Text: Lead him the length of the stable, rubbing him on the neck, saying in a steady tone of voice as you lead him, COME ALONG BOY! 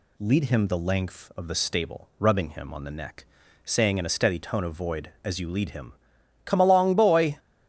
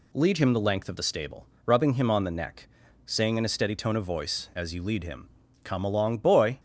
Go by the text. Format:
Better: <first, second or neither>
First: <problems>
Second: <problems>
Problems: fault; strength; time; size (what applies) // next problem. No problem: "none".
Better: second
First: says "void" for "voice"; at 4.7 s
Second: none